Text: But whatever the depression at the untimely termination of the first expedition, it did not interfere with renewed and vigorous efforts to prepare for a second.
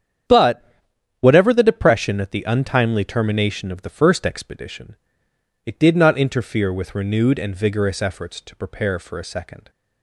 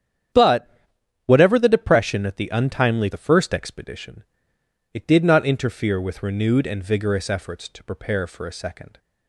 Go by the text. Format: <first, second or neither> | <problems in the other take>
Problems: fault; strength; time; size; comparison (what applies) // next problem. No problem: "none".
first | starts louder than the rest; strong; until 1.9 s; 9 dB; strong in the first // pauses between "But" and "whatever"; noticeable; at 0.6 s; 0.56 s long; noticeable in the first // skips "termination of"; at 3.1 s